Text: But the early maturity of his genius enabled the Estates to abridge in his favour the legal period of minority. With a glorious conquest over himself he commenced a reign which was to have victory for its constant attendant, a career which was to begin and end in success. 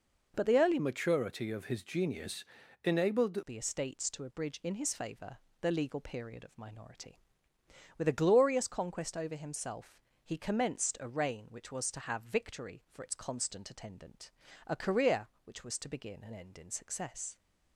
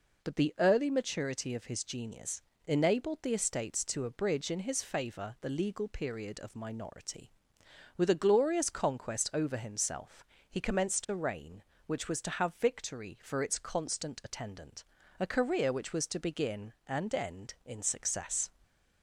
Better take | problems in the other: second | changes voice from "maturity" to "enabled"; from 0.7 to 3.4 s; 2.7 s long // pauses between "genius" and "enabled"; at 2.4 s; 0.40 s long; slight in the second // pauses between "favour" and "the"; slight; at 5.3 s; 0.24 s long // pauses between "himself" and "he"; slight; at 9.9 s; 0.24 s long; slight in the second

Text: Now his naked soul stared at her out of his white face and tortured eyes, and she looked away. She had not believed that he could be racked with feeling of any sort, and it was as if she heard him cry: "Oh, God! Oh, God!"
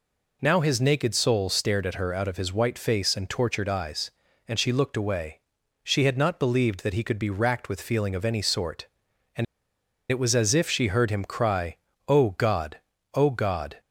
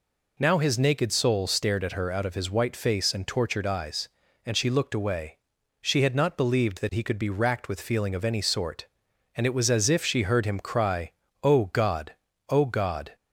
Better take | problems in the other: second | pauses between "and" and "it"; noticeable; at 9.4 s; 0.66 s long

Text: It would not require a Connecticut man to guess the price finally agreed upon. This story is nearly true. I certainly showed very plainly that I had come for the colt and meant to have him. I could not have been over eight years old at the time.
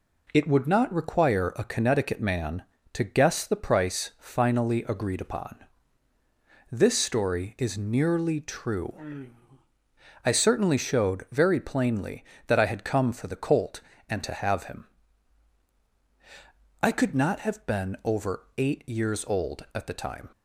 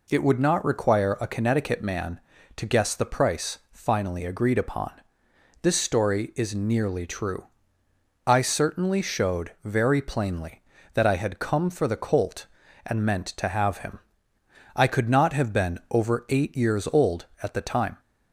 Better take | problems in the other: second | skips "meant"; at 14.2 s

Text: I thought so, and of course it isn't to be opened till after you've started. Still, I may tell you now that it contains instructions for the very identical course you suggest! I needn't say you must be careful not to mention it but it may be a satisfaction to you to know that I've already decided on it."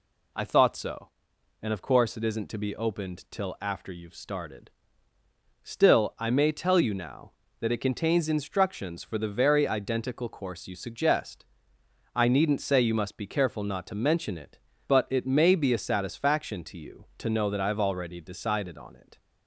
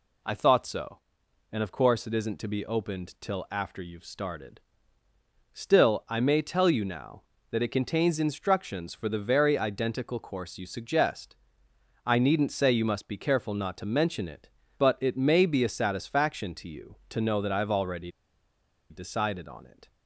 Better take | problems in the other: first | pauses between "already" and "decided"; noticeable; at 18.1 s; 0.79 s long

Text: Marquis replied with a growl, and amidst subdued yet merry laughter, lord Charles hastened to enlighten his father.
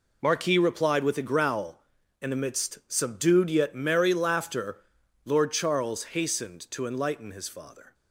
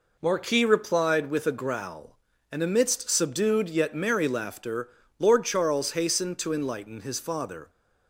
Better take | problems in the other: neither | none

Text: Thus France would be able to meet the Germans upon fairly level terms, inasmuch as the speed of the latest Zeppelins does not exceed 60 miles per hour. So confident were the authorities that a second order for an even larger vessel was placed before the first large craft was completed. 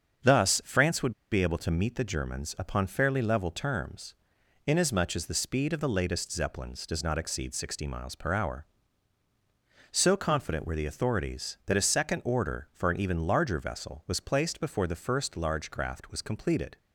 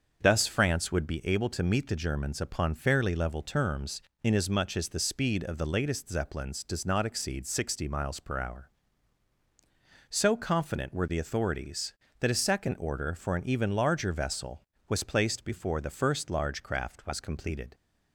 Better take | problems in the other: second | starts louder than the rest; strong; until 1.4 s; 7 dB; also in the second // pauses between "would" and "be"; slight; at 1.1 s; 0.20 s long

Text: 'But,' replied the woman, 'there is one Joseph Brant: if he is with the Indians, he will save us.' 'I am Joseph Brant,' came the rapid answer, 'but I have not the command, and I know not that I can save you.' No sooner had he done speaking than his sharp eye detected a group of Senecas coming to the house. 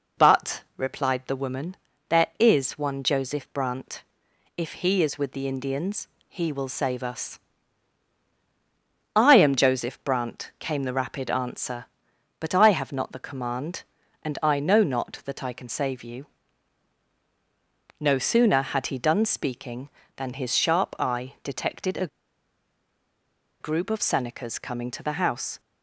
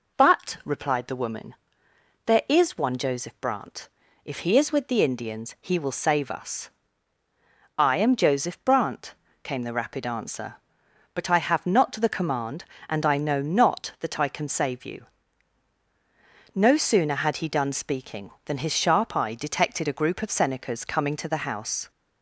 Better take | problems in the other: second | pauses between "a" and "group"; strong; at 22.0 s; 1.5 s long

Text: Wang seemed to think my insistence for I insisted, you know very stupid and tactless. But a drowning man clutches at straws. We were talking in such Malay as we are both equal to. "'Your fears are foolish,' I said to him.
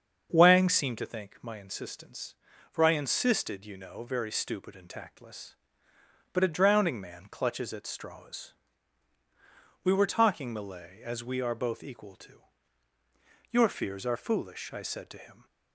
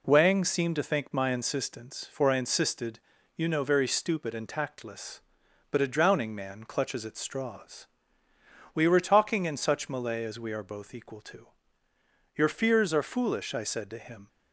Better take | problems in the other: second | starts louder than the rest; until 1.3 s; 7 dB // skips "in such"; at 10.5 s

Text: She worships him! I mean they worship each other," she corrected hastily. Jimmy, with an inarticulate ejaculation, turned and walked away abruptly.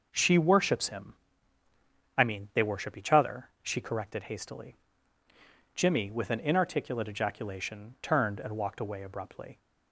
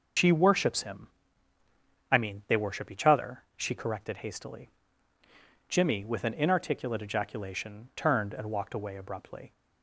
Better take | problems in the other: first | loses the start of "She"; at 0.1 s; 110 ms // starts louder than the rest; until 2.1 s; 7 dB

